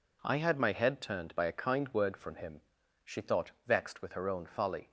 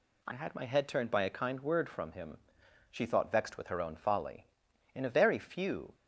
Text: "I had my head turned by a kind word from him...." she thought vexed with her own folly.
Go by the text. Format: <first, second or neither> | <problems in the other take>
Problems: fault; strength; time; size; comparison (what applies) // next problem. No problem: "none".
first | goes on to say "In a very few"; noticeable; from 4.9 s on; 1.0 s long